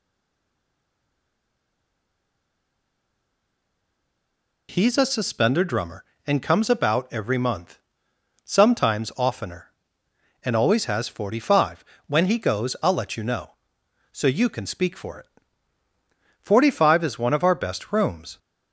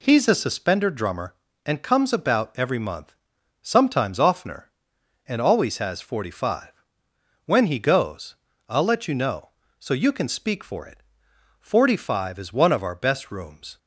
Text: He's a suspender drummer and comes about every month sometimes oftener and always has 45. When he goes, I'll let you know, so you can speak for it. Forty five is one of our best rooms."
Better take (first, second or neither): second